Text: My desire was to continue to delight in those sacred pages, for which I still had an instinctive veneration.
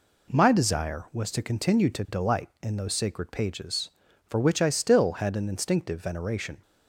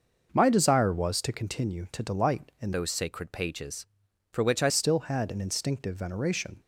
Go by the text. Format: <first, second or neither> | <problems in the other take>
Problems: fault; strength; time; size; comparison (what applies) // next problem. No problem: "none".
first | changes voice from "those" to "I"; from 2.7 to 4.7 s; 2.0 s long